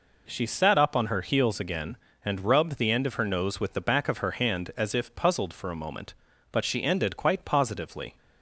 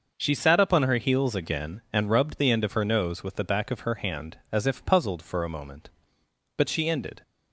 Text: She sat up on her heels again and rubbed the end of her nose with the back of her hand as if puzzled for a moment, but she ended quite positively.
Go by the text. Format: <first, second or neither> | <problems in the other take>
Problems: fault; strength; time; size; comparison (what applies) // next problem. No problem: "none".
first | starts louder than the rest; noticeable; until 1.1 s; 6 dB // stops before "quite positively"; at 7.2 s